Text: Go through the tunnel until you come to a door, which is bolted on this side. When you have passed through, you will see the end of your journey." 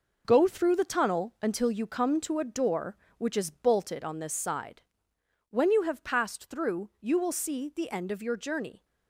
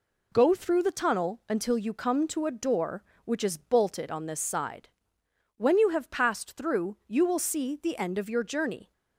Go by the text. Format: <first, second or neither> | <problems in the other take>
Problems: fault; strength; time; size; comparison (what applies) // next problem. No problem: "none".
second | gets quieter; strong; throughout; 7.5 dB